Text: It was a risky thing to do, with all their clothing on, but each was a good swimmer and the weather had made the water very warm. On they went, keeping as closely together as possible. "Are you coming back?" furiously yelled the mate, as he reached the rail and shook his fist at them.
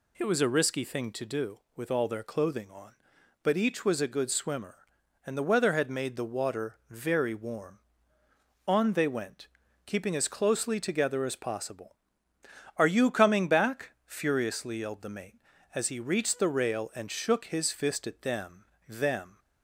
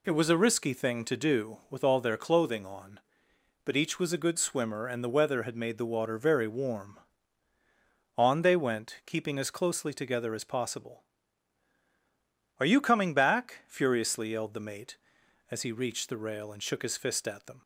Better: second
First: says "them" twice; at 18.8 s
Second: none

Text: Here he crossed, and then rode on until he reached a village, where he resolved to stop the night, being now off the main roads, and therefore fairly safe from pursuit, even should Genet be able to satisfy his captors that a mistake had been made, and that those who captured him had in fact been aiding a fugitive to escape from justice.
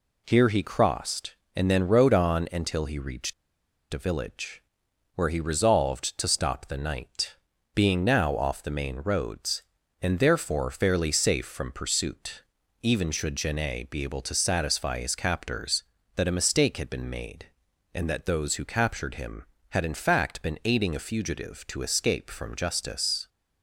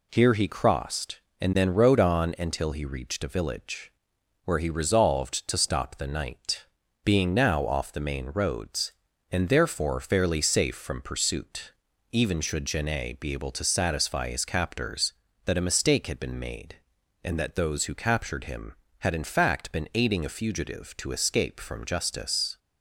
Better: second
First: pauses between "reached" and "a"; noticeable; at 3.3 s; 0.58 s long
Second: none

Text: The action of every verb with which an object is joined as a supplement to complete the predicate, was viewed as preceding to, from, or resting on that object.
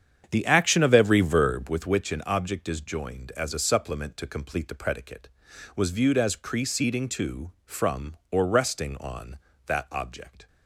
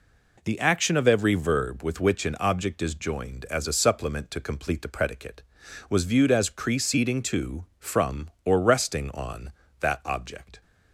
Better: second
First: starts louder than the rest; strong; until 1.9 s; 8 dB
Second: none

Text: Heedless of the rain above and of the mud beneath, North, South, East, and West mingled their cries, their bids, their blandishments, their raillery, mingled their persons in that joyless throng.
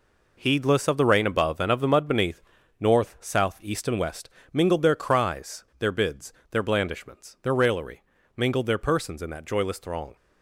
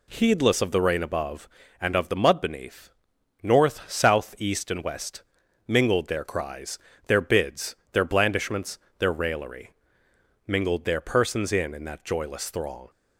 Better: first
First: pauses between "West" and "mingled"; slight; at 4.2 s; 0.24 s long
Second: pauses between "West" and "mingled"; at 5.2 s; 0.44 s long // says "in" twice; at 11.7 s

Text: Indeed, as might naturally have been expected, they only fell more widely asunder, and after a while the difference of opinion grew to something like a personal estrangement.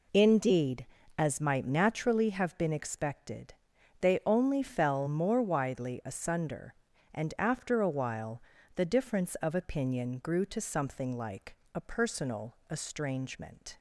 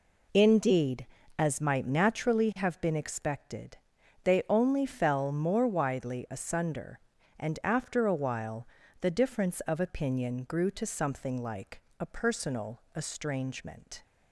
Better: neither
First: pauses between "while" and "the"; slight; at 8.4 s; 0.36 s long // pauses between "like" and "a"; slight; at 11.5 s; 0.18 s long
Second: pauses between "while" and "the"; slight; at 8.6 s; 0.36 s long // pauses between "like" and "a"; slight; at 11.8 s; 0.18 s long

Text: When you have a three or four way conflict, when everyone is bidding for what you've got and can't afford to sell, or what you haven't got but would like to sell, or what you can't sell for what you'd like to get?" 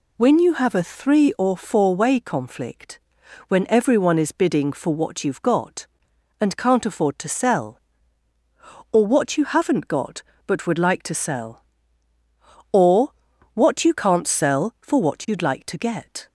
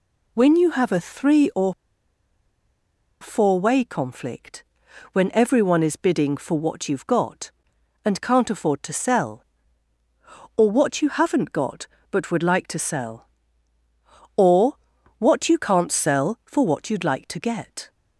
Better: first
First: pauses between "or" and "what"; at 13.0 s; 0.42 s long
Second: pauses between "or" and "four"; strong; at 1.7 s; 1.4 s long // pauses between "or" and "what"; at 14.7 s; 0.42 s long

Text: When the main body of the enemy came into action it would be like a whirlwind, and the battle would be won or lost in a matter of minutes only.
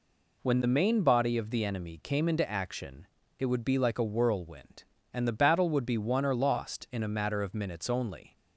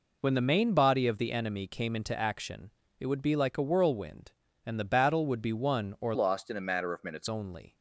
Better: first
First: pauses between "action" and "it"; slight; at 3.0 s; 0.32 s long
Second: pauses between "action" and "it"; slight; at 2.7 s; 0.28 s long // changes voice from "lost" to "minutes"; from 6.1 to 7.2 s; 1.1 s long

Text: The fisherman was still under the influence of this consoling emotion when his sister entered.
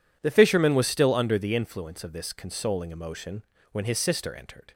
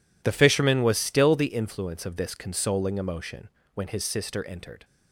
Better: first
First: pauses between "emotion" and "when"; slight; at 3.4 s; 0.26 s long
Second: skips "under"; at 1.3 s // pauses between "emotion" and "when"; slight; at 3.4 s; 0.26 s long

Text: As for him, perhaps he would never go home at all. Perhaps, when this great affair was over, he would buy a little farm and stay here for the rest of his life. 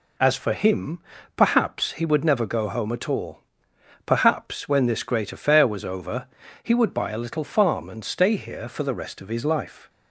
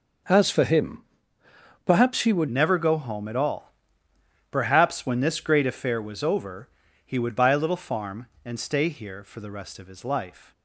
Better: first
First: none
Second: starts louder than the rest; noticeable; until 2.1 s; 6 dB // changes voice at "never"; from 2.4 s on; 8.1 s long

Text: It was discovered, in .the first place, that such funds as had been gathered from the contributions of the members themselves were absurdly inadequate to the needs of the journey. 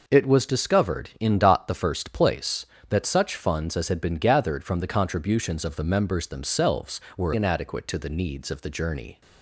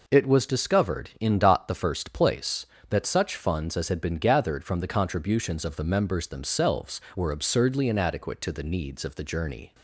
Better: second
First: skips "absurdly"; at 7.3 s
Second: none

